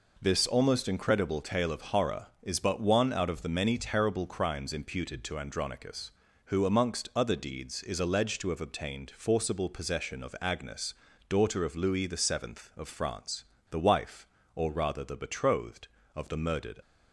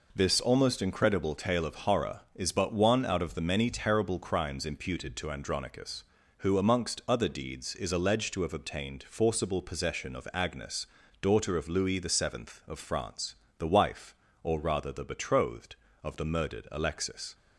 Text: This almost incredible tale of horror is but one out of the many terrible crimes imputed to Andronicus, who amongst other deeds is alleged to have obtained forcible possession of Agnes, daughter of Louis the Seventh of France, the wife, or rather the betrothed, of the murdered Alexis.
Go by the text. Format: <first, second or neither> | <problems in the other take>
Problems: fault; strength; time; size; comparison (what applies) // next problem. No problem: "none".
second | stops before "Alexis"; at 16.8 s